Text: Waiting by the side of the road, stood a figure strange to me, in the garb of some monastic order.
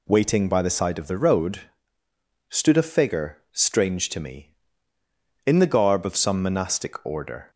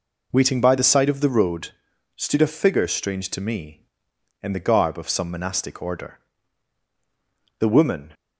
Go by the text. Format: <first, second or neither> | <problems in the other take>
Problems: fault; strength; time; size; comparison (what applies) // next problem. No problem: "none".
first | goes on to say "The woman"; from 7.5 s on; 0.54 s long